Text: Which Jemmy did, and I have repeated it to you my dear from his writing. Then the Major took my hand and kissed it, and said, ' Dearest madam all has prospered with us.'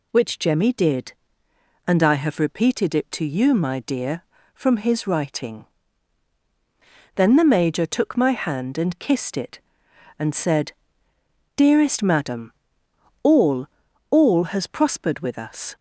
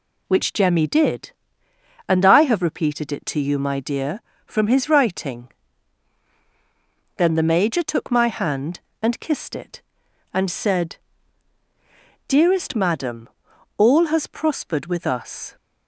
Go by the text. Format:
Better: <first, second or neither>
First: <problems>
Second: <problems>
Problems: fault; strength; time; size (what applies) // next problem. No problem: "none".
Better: second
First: pauses between "madam" and "all"; noticeable; at 12.5 s; 0.70 s long // says "all" twice; at 14.0 s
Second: pauses between "madam" and "all"; noticeable; at 13.2 s; 0.50 s long